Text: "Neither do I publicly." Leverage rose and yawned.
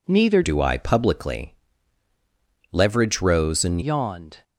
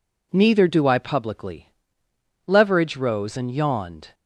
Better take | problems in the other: second | changes voice from "do" to "and"; from 0.4 to 3.8 s; 3.4 s long

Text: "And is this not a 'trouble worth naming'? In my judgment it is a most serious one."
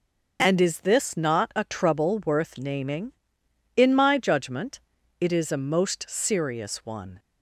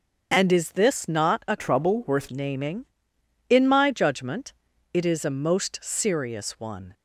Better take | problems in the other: first | starts louder than the rest; until 1.3 s; 6.5 dB // changes voice from "trouble" to "worth"; from 1.5 to 2.2 s; 0.7 s long // pauses between "judgment" and "it"; at 4.5 s; 0.40 s long; also in the first

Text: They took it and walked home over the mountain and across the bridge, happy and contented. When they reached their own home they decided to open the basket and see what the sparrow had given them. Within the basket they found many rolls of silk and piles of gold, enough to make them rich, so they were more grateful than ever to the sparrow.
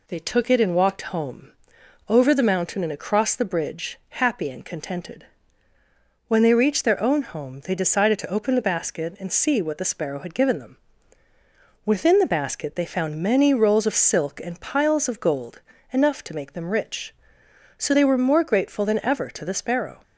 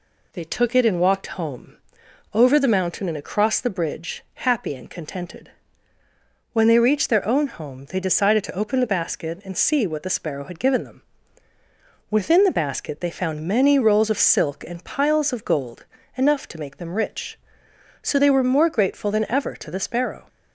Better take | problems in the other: neither | pauses between "home" and "over"; noticeable; the same in both

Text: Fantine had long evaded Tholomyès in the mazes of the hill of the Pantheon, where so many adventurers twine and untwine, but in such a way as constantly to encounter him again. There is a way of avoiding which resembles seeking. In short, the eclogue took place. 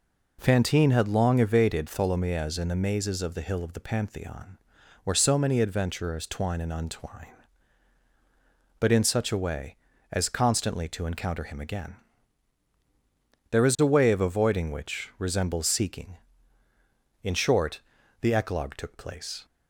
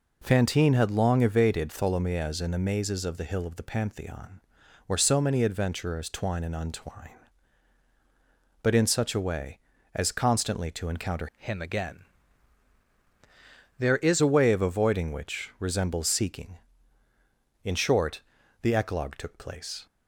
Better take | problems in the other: first | changes voice from "him" to "is"; from 11.3 to 14.2 s; 2.9 s long

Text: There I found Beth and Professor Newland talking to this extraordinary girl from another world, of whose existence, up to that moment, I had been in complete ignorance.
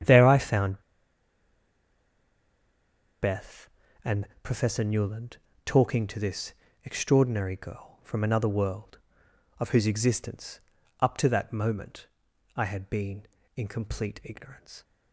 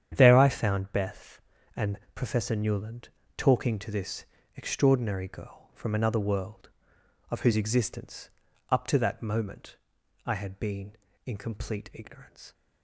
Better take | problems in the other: second | starts louder than the rest; strong; until 3.4 s; 9 dB; strong in the second // pauses between "found" and "Beth"; strong; at 0.8 s; 2.3 s long // pauses between "and" and "Professor"; slight; at 4.2 s; 0.16 s long; slight in the second // pauses between "Newland" and "talking"; slight; at 5.3 s; 0.26 s long; slight in the second // pauses between "this" and "extraordinary"; slight; at 6.5 s; 0.28 s long; slight in the second

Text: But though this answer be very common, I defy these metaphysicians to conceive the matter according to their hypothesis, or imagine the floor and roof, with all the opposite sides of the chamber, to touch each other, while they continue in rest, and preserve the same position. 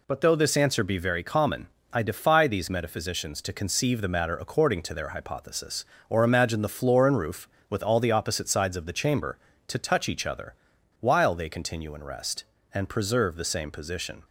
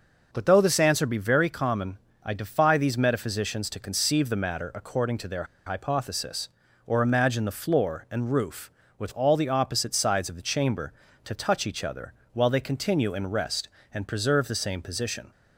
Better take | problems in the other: first | pauses between "their" and "hypothesis"; slight; at 5.4 s; 0.21 s long

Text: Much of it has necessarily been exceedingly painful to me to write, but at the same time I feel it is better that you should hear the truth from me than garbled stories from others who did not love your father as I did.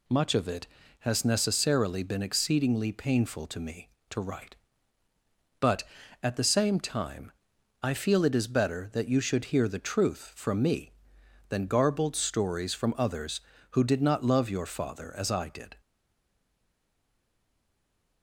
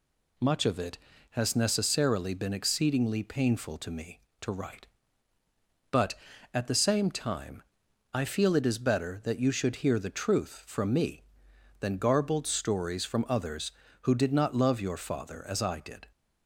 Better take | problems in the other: second | pauses between "time" and "I"; noticeable; at 7.3 s; 0.50 s long; noticeable in the second // stays silent after the last word; from 15.7 s on; 2.5 s long

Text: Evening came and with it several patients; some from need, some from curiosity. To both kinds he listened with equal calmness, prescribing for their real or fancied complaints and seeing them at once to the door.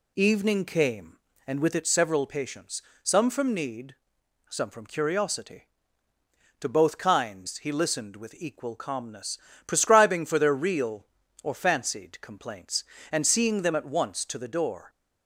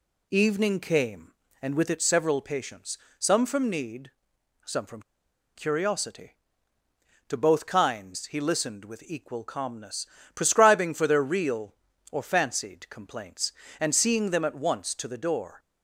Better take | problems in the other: first | pauses between "from" and "curiosity"; noticeable; at 5.0 s; 0.55 s long

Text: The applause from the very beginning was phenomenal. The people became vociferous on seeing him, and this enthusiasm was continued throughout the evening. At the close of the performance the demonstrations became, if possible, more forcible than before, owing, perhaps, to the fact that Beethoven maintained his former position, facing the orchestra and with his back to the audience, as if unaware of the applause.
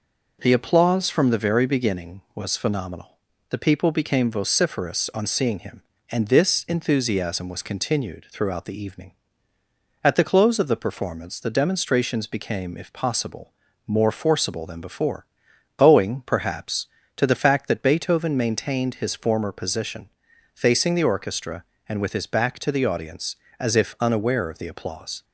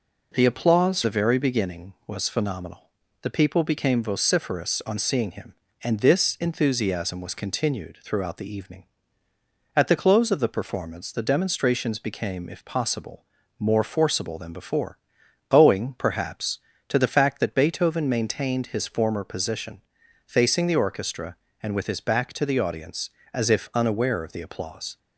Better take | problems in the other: first | skips "from"; at 1.0 s

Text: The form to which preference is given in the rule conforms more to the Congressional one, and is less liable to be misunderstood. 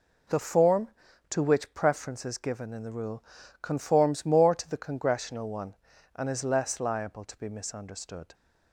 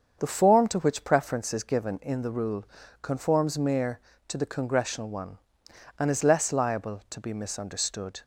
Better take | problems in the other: first | starts louder than the rest; until 1.2 s; 7 dB // pauses between "rule" and "conforms"; slight; at 2.6 s; 0.36 s long; also in the first // says "mere" for "more"; at 3.5 s

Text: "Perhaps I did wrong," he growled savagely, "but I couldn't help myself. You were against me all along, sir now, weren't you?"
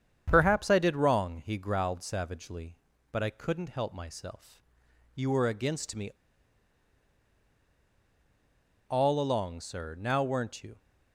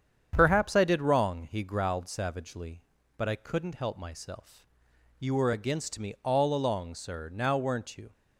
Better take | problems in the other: second | starts louder than the rest; strong; until 1.2 s; 8 dB; strong in the second // pauses between "me" and "all"; strong; at 6.1 s; 2.7 s long

